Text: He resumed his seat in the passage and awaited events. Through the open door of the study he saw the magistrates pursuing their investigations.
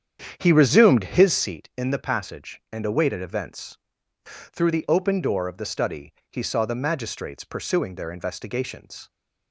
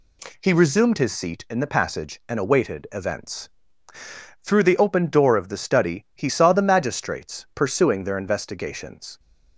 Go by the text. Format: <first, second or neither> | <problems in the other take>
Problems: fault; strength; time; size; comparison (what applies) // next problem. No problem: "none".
second | starts louder than the rest; strong; until 1.5 s; 9 dB // pauses between "study" and "he"; slight; at 6.1 s; 0.20 s long